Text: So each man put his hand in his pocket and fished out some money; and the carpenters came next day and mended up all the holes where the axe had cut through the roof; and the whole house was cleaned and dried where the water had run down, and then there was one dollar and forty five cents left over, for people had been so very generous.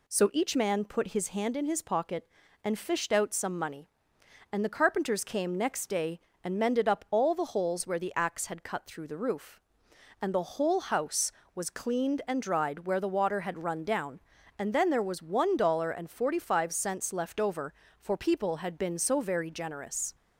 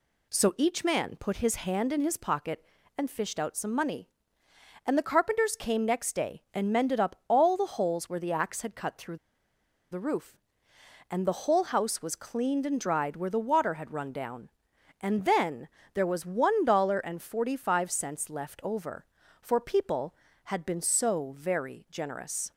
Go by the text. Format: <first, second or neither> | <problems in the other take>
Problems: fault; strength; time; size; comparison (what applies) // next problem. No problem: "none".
first | pauses between "through" and "the"; noticeable; at 9.1 s; 0.75 s long // pauses between "then" and "there"; slight; at 15.6 s; 0.26 s long